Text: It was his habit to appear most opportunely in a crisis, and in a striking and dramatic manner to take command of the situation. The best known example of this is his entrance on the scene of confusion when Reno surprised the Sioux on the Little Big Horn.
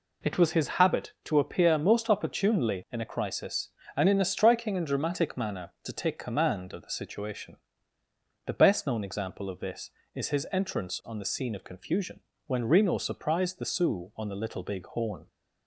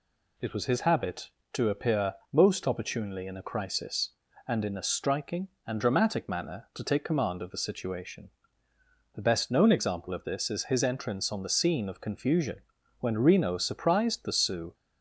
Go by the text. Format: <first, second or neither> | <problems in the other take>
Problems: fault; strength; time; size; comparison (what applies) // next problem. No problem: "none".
first | pauses between "appear" and "most"; slight; at 2.1 s; 0.18 s long // pauses between "confusion" and "when"; at 12.5 s; 0.40 s long; slight in the first // stops before "on the Little Big Horn"; at 14.7 s